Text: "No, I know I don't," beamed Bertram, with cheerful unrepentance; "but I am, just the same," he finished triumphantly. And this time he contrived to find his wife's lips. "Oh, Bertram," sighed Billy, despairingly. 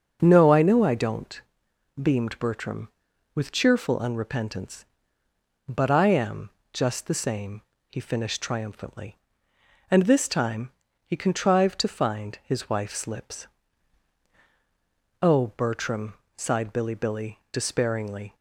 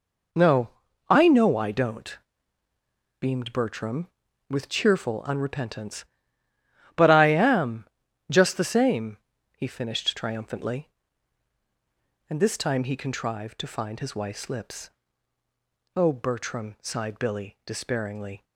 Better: second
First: starts louder than the rest; until 1.2 s; 6.5 dB // pauses between "time" and "he"; slight; at 10.7 s; 0.36 s long // says "Billy" twice; at 16.9 s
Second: none

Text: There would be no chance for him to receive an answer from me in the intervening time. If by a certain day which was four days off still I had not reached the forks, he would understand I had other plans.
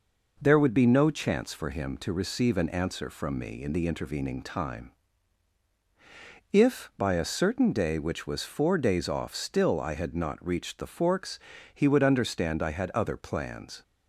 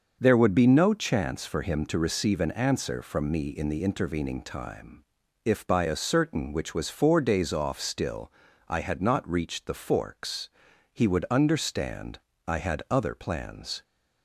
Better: first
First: none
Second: starts louder than the rest; until 1.2 s; 6.5 dB // skips "day"; at 6.5 s // pauses between "still" and "I"; slight; at 8.3 s; 0.34 s long // pauses between "understand" and "I"; slight; at 12.1 s; 0.30 s long

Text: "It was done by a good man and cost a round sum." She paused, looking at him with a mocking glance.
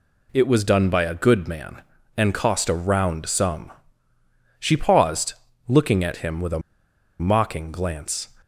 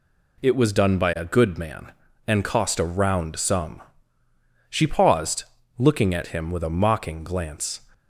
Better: second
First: pauses between "a" and "mocking"; noticeable; at 6.6 s; 0.59 s long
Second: none

